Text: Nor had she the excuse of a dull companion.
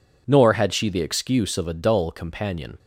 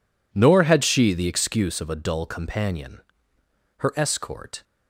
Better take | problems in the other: first | goes on to say "Her escort"; noticeable; from 3.7 s on; 0.86 s long

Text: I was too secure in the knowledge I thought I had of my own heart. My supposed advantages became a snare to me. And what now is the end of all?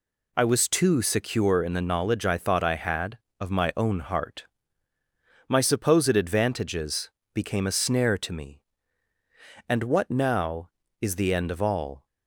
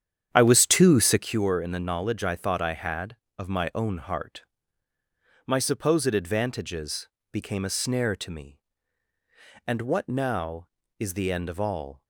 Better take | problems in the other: first | starts louder than the rest; strong; until 1.4 s; 9 dB // pauses between "advantages" and "became"; slight; at 7.0 s; 0.24 s long; slight in the first

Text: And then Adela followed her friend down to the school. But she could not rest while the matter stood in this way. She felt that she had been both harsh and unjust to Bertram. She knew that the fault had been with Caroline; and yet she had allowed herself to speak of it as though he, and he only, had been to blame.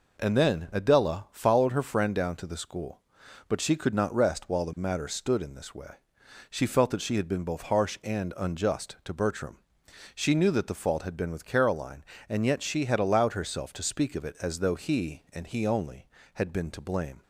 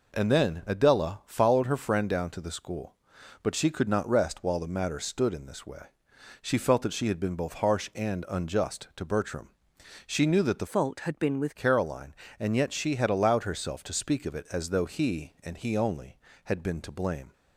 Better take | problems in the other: first | changes voice from "fault" to "with"; from 10.6 to 11.5 s; 0.9 s long

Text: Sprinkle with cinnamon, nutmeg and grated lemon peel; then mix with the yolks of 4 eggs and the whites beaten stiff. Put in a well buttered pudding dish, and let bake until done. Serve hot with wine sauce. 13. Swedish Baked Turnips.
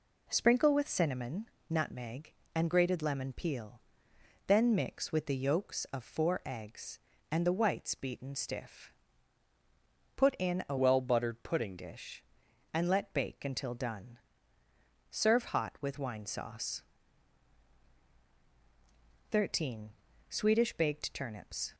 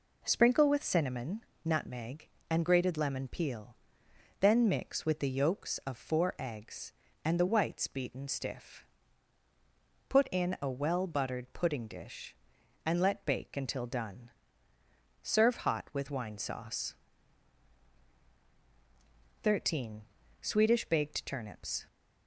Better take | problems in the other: second | changes voice from "well" to "pudding"; from 10.7 to 11.7 s; 1.0 s long

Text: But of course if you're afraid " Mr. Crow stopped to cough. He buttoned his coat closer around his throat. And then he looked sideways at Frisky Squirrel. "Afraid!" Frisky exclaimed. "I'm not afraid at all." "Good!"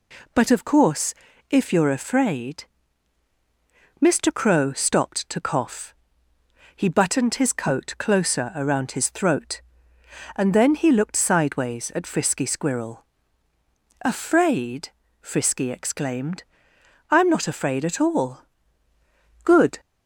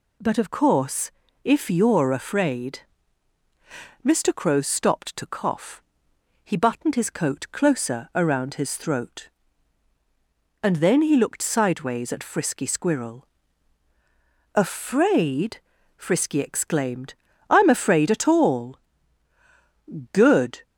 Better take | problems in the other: first | pauses between "course" and "if"; slight; at 1.1 s; 0.32 s long; slight in the first // skips "not"; at 17.6 s

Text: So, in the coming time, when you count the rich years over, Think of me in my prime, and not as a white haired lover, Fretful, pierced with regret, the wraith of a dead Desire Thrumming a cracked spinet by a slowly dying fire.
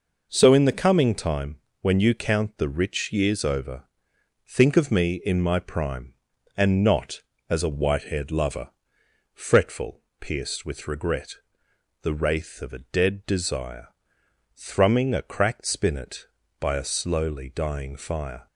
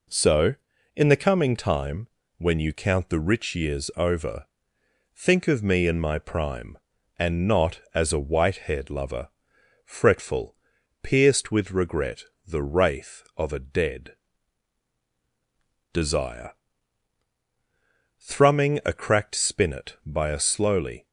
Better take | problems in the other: first | pauses between "dead" and "Desire"; strong; at 14.1 s; 1.7 s long // pauses between "Desire" and "Thrumming"; strong; at 16.5 s; 1.6 s long; noticeable in the first // stops before "dying fire"; at 21.0 s

